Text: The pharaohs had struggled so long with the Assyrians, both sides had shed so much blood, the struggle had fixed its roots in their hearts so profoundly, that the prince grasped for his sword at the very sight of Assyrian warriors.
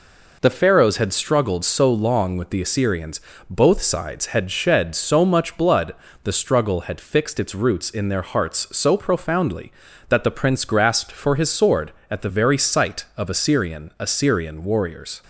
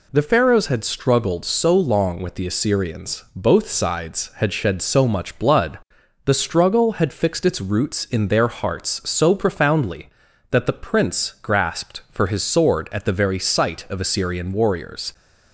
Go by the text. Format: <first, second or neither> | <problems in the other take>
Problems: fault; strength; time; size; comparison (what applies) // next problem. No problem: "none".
second | says "Assyrian" twice; at 13.9 s